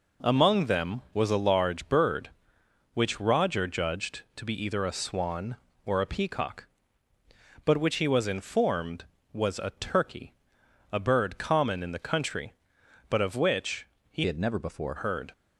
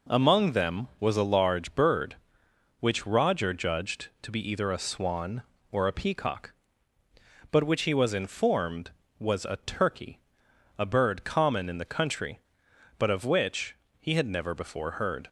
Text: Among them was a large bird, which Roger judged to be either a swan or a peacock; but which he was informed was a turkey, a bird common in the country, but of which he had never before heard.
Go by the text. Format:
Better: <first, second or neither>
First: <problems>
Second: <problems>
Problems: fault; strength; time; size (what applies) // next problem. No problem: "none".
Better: second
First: pauses between "which" and "he"; slight; at 13.8 s; 0.24 s long // changes voice from "had" to "before"; from 14.2 to 14.9 s; 0.7 s long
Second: pauses between "which" and "he"; slight; at 13.7 s; 0.24 s long